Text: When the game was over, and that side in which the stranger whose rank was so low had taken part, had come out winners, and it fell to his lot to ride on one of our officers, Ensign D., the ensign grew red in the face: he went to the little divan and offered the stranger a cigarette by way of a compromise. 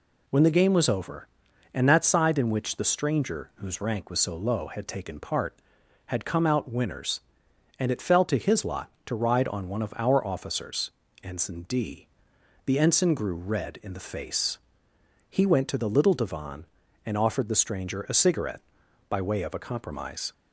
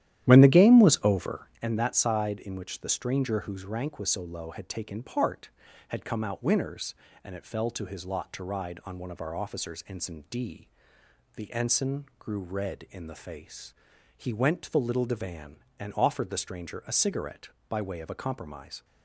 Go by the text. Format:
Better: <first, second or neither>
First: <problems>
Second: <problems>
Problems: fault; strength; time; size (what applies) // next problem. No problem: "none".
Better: first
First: none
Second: starts louder than the rest; strong; until 1.7 s; 12 dB // pauses between "ensign" and "grew"; slight; at 12.0 s; 0.16 s long